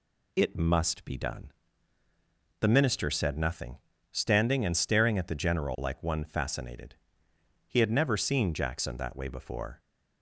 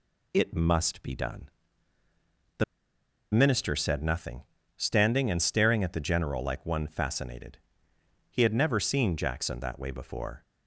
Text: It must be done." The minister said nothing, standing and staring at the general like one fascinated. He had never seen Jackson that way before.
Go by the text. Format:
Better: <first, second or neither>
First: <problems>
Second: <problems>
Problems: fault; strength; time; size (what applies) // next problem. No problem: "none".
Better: first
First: none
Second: pauses between "The" and "minister"; noticeable; at 2.6 s; 0.68 s long